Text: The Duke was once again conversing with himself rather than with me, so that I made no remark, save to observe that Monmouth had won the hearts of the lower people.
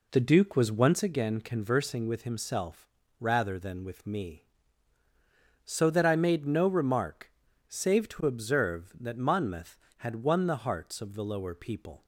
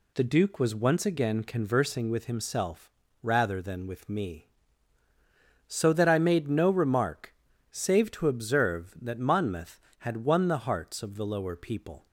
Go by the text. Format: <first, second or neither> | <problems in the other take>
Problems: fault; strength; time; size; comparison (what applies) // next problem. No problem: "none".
second | starts louder than the rest; slight; until 1.1 s; 3 dB // pauses between "himself" and "rather"; slight; at 2.8 s; 0.32 s long; slight in the second